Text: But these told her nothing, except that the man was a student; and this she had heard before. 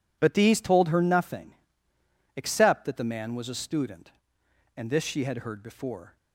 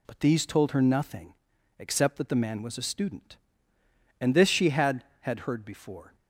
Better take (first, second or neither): first